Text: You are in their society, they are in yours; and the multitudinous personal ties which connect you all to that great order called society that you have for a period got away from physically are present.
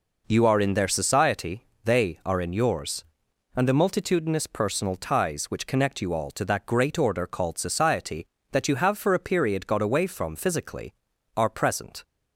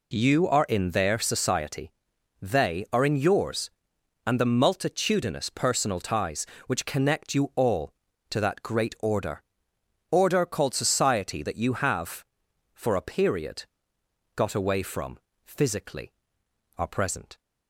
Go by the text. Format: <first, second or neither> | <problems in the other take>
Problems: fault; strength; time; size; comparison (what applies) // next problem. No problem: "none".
first | says "order" twice; at 10.1 s // pauses between "period" and "got"; noticeable; at 13.6 s; 0.72 s long // pauses between "from" and "physically"; slight; at 15.1 s; 0.30 s long